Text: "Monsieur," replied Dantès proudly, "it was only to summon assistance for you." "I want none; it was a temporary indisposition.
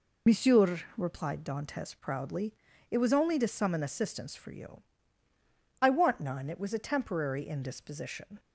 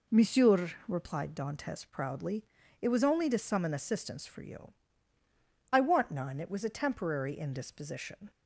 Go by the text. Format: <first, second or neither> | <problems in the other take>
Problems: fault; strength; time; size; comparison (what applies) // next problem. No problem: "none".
second | loses the start of "Monsieur"; at 0.2 s; 70 ms